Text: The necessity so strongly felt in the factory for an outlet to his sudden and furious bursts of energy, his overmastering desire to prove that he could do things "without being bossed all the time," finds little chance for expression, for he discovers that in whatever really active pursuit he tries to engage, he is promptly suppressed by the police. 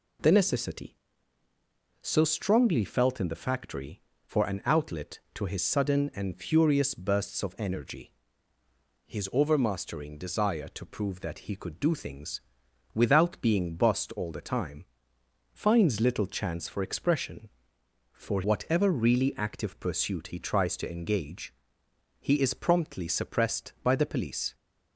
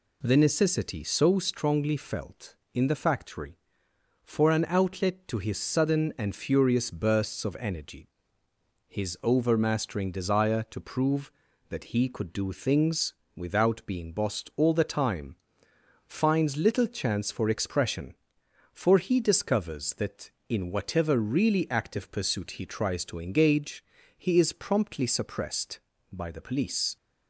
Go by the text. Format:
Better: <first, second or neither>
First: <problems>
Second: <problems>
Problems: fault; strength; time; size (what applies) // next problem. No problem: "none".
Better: second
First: pauses between "things" and "without"; noticeable; at 12.4 s; 0.52 s long // skips "he discovers that in"; at 18.4 s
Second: pauses between "things" and "without"; slight; at 13.1 s; 0.22 s long